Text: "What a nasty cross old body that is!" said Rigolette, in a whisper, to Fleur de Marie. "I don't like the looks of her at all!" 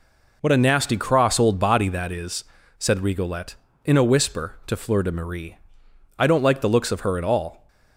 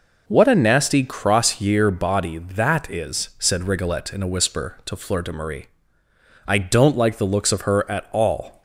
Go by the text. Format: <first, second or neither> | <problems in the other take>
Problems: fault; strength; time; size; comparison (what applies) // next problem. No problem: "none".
first | says "year" for "old"; at 1.5 s